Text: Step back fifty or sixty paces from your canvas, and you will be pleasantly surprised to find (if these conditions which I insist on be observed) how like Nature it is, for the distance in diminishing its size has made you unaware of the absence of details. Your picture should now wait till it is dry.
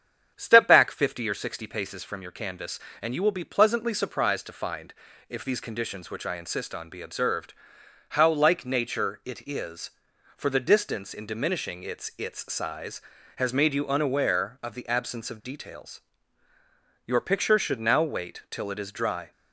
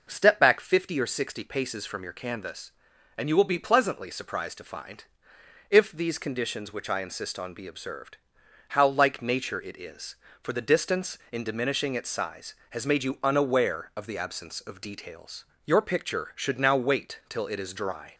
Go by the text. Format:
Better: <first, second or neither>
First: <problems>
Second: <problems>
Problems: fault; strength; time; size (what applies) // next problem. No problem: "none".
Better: second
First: starts louder than the rest; strong; until 1.3 s; 8 dB // says "its" twice; at 12.1 s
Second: none